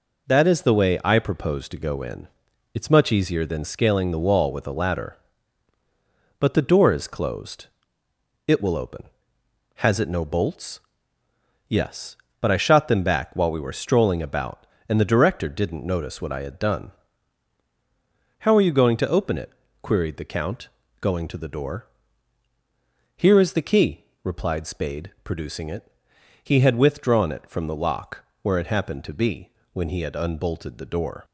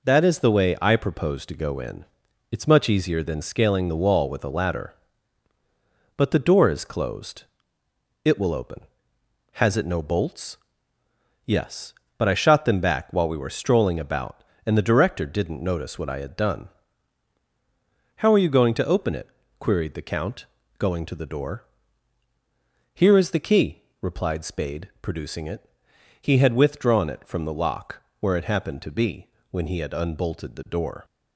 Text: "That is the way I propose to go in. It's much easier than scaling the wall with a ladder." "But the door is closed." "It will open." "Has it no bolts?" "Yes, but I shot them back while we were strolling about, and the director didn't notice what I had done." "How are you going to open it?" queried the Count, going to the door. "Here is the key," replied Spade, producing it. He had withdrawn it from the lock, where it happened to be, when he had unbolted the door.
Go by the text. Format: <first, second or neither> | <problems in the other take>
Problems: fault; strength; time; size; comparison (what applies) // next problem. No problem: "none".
neither | none